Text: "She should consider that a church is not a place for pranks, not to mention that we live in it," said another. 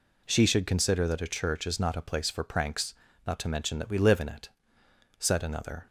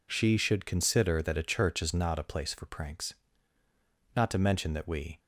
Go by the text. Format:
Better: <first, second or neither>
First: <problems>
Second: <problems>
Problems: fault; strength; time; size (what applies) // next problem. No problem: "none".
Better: first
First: none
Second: stops before "live in it said another"; at 5.1 s